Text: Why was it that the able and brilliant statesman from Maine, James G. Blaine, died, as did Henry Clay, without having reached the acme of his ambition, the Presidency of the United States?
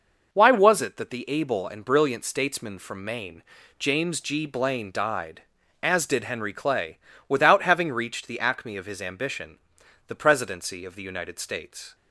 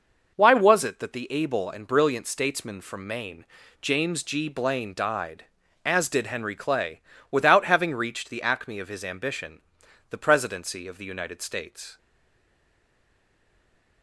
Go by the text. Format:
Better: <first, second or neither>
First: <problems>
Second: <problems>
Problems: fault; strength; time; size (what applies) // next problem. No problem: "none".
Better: first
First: none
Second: stays silent after the last word; noticeable; from 11.9 s on; 2.1 s long